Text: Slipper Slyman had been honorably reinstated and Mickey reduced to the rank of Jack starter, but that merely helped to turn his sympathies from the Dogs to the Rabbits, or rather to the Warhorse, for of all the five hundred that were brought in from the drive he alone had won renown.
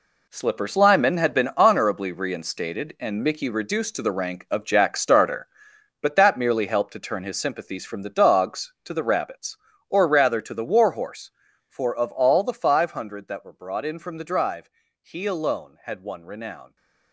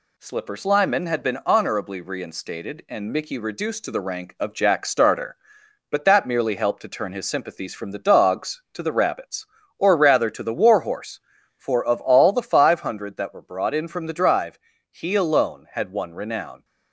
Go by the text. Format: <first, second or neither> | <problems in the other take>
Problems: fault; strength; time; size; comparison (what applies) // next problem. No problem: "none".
second | gets quieter; strong; throughout; 10.5 dB // pauses between "drive" and "he"; slight; at 14.6 s; 0.32 s long; slight in the second